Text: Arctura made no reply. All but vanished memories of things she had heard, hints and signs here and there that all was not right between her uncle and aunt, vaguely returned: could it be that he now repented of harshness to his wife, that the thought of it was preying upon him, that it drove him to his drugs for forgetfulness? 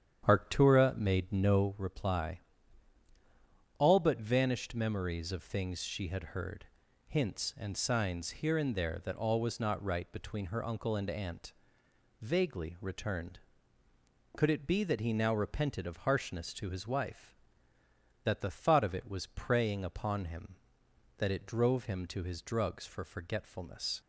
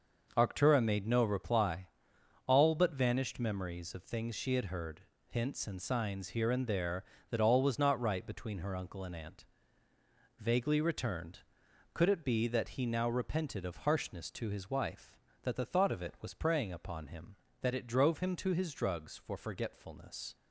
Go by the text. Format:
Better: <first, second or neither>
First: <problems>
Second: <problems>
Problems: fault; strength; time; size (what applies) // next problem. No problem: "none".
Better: second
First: starts louder than the rest; strong; until 1.7 s; 9 dB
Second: none